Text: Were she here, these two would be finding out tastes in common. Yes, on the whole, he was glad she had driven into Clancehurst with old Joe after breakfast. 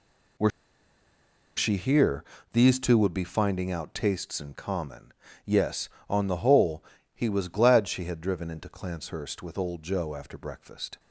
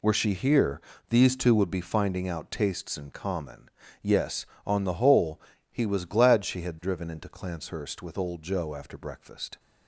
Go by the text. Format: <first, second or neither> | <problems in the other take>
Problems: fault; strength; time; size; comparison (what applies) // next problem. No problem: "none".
second | pauses between "Were" and "she"; at 0.4 s; 1.0 s long